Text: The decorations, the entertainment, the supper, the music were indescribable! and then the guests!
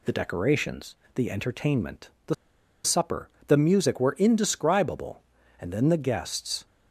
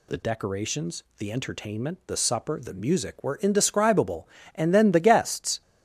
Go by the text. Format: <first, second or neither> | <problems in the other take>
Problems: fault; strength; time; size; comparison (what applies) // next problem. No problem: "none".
second | pauses between "the" and "supper"; noticeable; at 2.3 s; 0.50 s long